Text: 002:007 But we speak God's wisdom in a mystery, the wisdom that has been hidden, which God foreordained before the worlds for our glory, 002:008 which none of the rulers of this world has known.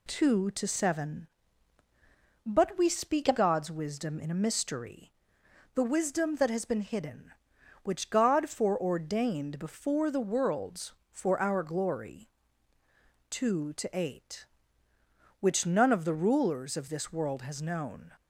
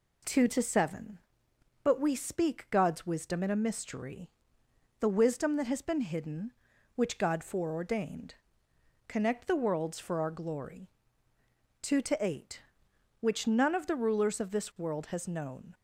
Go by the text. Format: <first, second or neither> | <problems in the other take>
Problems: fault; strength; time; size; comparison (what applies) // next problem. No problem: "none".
first | says "connect" for "before"; at 9.0 s